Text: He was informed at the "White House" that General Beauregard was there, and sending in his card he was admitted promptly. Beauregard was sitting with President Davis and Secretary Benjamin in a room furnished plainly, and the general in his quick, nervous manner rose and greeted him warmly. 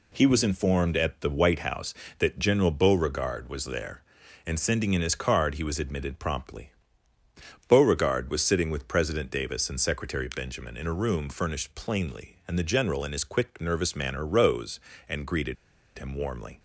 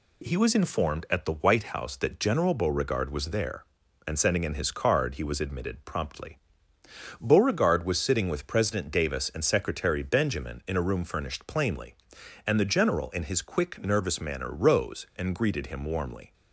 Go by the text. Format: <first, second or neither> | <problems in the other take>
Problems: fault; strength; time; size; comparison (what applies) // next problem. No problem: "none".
second | pauses between "greeted" and "him"; at 15.5 s; 0.41 s long